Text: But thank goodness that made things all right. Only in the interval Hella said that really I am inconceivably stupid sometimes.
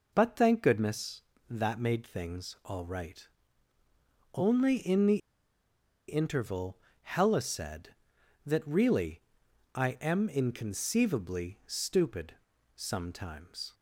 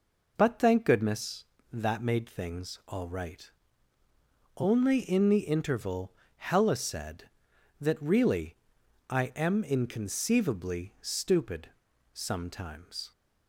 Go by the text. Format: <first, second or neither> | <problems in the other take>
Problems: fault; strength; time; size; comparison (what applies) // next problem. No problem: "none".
second | pauses between "the" and "interval"; noticeable; at 5.1 s; 0.90 s long // pauses between "interval" and "Hella"; slight; at 6.7 s; 0.24 s long; slight in the second // pauses between "really" and "I"; noticeable; at 9.1 s; 0.54 s long; noticeable in the second // pauses between "stupid" and "sometimes"; at 12.3 s; 0.42 s long; also in the second